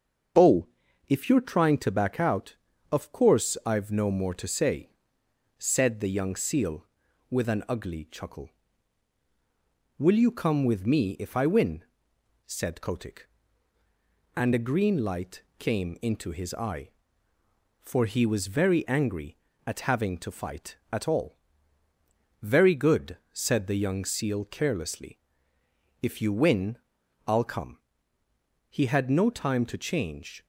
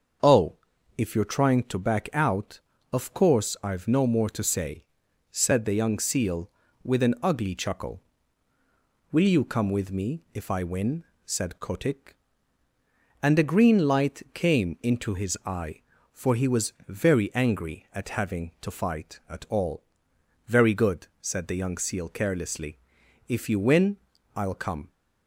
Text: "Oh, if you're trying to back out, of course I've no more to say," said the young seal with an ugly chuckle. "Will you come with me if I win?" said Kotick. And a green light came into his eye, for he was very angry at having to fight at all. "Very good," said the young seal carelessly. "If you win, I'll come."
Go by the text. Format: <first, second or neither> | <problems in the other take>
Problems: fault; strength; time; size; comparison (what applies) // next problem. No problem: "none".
second | starts louder than the rest; noticeable; until 1.8 s; 6 dB; also in the second // pauses between "light" and "came"; slight; at 15.4 s; 0.16 s long // goes on to say "He had no time to change"; strong; from 28.6 s on; 1.7 s long